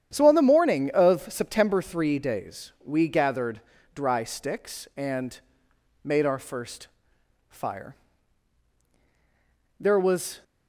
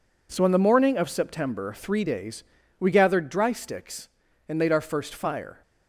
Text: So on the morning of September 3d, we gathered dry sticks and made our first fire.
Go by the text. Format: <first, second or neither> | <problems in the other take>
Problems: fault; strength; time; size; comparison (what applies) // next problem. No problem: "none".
second | starts louder than the rest; strong; until 1.1 s; 9.5 dB // pauses between "gathered" and "dry"; slight; at 3.6 s; 0.32 s long // pauses between "and" and "made"; noticeable; at 5.3 s; 0.64 s long // pauses between "first" and "fire"; noticeable; at 6.8 s; 0.62 s long // goes on to say "There was"; noticeable; from 9.8 s on; 0.62 s long